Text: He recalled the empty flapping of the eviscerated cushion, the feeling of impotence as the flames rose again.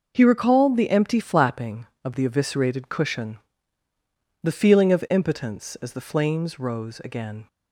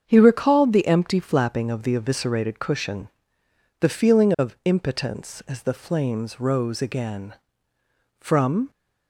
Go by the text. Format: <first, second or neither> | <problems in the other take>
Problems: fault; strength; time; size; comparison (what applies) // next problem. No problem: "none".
first | starts louder than the rest; strong; until 1.0 s; 7 dB // goes on to say "From"; from 8.1 s on; 0.50 s long